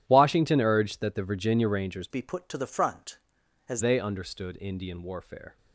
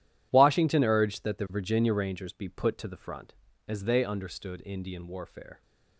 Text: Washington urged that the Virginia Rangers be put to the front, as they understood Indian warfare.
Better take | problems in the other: second | changes voice from "be" to "as"; from 2.1 to 3.8 s; 1.7 s long

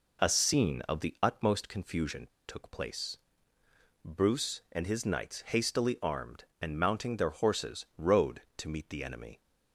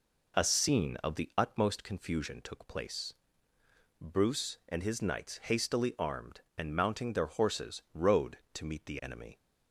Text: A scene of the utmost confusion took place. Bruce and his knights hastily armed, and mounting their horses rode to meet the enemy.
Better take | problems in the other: second | pauses between "confusion" and "took"; slight; at 2.2 s; 0.21 s long

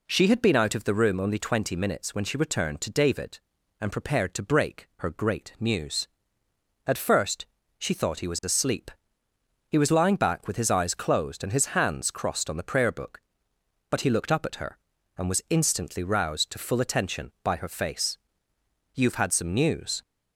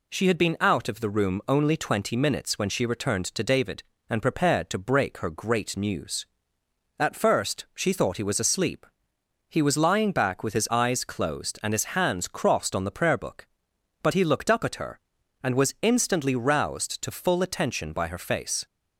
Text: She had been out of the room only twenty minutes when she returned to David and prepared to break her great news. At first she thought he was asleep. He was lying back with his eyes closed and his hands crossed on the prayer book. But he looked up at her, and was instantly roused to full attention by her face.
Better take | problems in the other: second | pauses between "first" and "she"; slight; at 7.4 s; 0.32 s long // goes on to say "You've had some news"; noticeable; from 18.9 s on; 1.0 s long

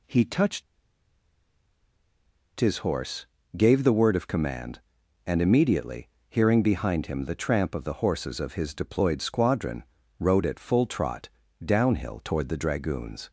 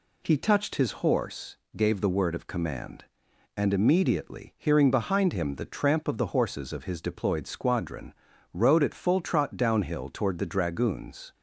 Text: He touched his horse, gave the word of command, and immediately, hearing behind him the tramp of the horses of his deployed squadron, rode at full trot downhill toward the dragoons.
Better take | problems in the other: second | pauses between "touched" and "his"; strong; at 0.6 s; 1.9 s long // pauses between "trot" and "downhill"; slight; at 11.2 s; 0.36 s long

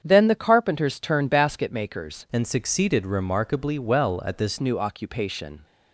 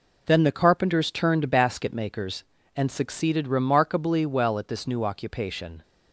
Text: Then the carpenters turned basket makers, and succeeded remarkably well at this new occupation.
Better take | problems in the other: second | starts louder than the rest; strong; until 1.0 s; 8 dB // changes voice from "and" to "this"; from 2.3 to 4.5 s; 2.2 s long

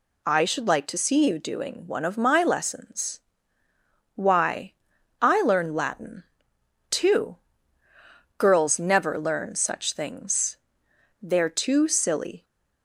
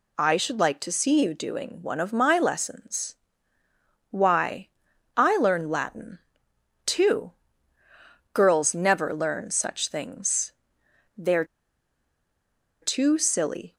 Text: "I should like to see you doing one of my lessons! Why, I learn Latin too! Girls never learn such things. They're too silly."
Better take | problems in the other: first | pauses between "Latin" and "too"; noticeable; at 6.1 s; 0.66 s long; noticeable in the first // pauses between "They're" and "too"; strong; at 11.4 s; 1.3 s long

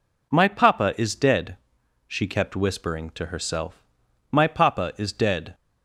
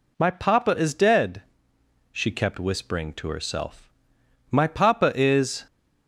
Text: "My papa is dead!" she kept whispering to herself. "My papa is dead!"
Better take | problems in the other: first | stops before "dead"; at 5.6 s

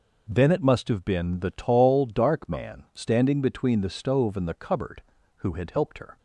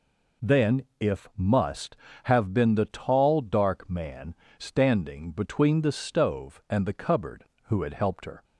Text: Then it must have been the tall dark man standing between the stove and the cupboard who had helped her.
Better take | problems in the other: first | says "if" for "it"; at 0.9 s // pauses between "man" and "standing"; slight; at 4.3 s; 0.24 s long

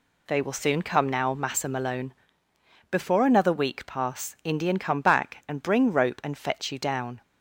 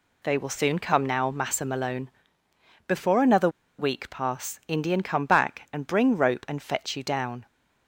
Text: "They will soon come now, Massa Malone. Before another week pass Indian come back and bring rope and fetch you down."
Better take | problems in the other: first | pauses between "another" and "week"; slight; at 3.4 s; 0.29 s long

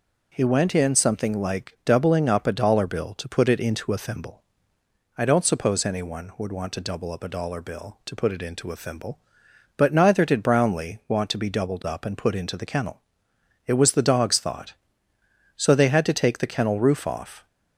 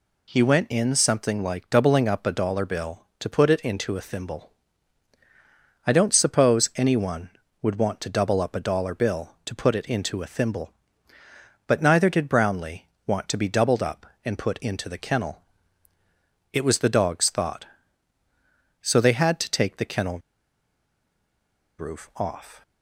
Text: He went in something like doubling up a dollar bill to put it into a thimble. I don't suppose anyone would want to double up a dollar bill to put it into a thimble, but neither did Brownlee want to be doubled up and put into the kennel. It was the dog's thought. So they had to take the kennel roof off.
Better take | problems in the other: first | pauses between "Brownlee" and "want"; slight; at 12.8 s; 0.22 s long // pauses between "kennel" and "roof"; strong; at 20.1 s; 1.5 s long

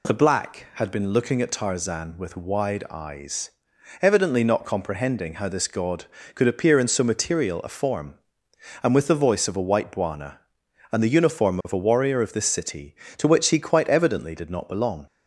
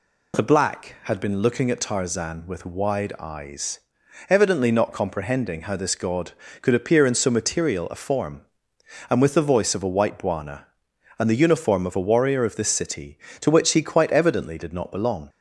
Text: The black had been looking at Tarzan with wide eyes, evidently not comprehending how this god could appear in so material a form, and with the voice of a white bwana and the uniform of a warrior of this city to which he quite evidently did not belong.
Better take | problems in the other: neither | none

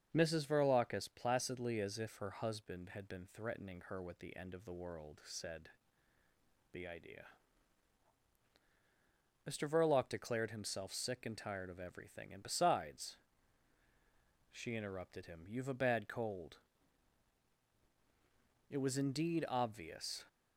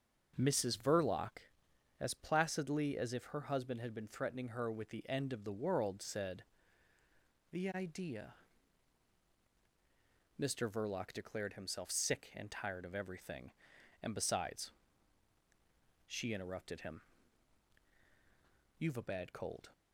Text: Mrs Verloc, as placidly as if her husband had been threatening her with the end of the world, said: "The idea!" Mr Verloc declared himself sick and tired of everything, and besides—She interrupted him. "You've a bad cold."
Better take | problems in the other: second | starts louder than the rest; until 1.1 s; 6.5 dB; also in the second // goes on to say "It was indeed obvious"; from 18.6 s on; 1.5 s long

